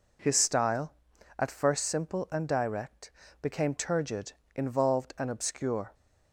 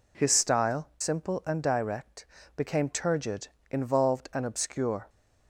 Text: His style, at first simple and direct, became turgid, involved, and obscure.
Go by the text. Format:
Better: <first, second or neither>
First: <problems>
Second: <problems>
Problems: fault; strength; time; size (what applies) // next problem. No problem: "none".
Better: first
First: none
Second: skips "at first"; at 0.9 s